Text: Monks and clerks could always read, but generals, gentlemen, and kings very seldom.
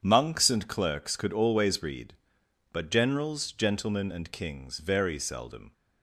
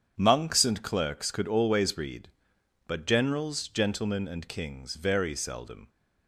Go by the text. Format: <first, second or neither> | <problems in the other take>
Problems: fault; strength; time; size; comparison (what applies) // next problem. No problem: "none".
neither | starts louder than the rest; strong; the same in both